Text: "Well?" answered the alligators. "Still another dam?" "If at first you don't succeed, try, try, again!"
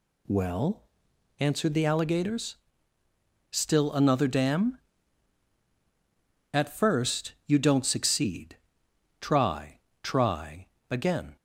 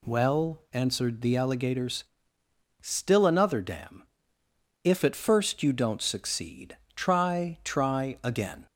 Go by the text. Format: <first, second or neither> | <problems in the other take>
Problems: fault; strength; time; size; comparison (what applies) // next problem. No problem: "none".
second | skips "If"; at 5.6 s